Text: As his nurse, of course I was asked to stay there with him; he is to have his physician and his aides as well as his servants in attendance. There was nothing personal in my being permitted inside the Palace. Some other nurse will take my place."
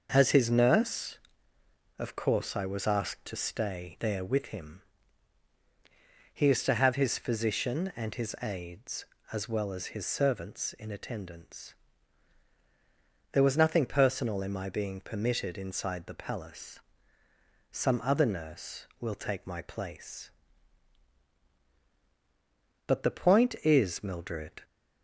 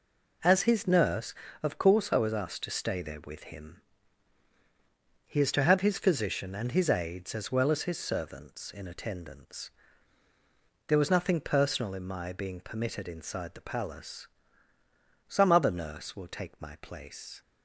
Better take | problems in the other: second | starts louder than the rest; noticeable; until 1.1 s; 6 dB // goes on to say "But the point is Mildred"; strong; from 22.8 s on; 1.7 s long

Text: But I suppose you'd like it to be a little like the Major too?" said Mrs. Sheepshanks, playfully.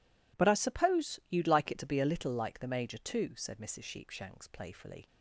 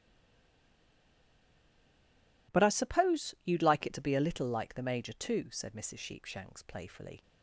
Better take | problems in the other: first | stays silent before the first word; until 2.4 s; 2.4 s long

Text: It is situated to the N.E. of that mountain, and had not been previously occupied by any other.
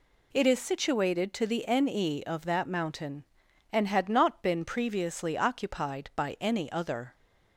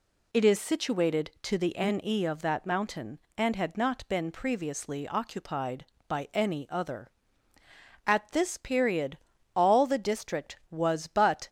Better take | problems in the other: first | goes on to say "At this period all the district was but"; strong; from 8.0 s on; 3.4 s long

